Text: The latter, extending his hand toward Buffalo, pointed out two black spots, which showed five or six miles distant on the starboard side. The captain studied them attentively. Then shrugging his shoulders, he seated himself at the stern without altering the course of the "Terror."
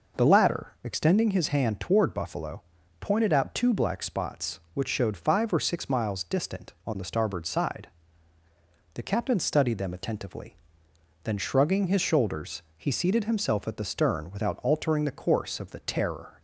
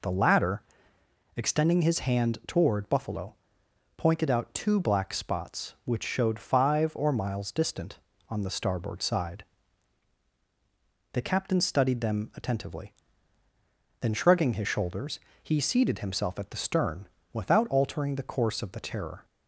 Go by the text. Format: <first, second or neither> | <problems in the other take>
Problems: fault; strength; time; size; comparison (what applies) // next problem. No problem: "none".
first | skips "six"; at 7.1 s // pauses between "stern" and "without"; slight; at 17.0 s; 0.26 s long